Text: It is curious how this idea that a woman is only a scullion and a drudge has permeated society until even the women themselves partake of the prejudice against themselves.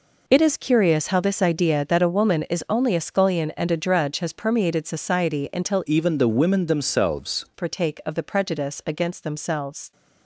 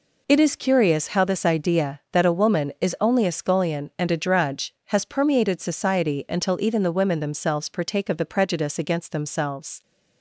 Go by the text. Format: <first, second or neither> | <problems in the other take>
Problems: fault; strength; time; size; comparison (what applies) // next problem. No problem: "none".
second | changes voice from "even" to "themselves"; from 5.8 to 7.4 s; 1.6 s long